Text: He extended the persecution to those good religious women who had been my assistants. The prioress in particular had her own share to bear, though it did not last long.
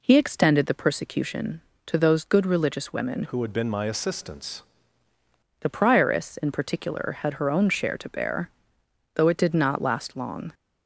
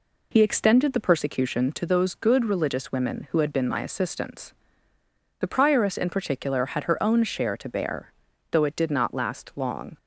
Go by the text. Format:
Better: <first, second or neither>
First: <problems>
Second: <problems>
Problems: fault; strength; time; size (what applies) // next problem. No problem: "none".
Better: second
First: changes voice from "who" to "assistants"; from 3.2 to 4.6 s; 1.4 s long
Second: none